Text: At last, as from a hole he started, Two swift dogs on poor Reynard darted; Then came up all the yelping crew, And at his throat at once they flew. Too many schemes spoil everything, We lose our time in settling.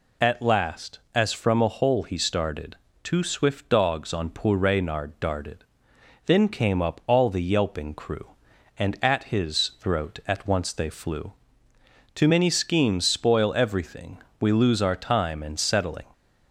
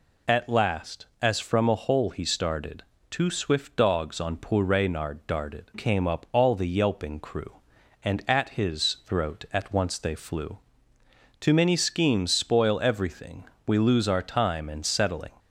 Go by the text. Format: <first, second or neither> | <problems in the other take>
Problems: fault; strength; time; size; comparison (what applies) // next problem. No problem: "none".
first | skips "Then"; at 5.7 s